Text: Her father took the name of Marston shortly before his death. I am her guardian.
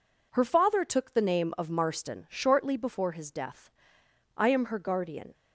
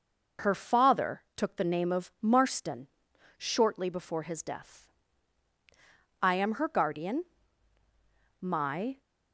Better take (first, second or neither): first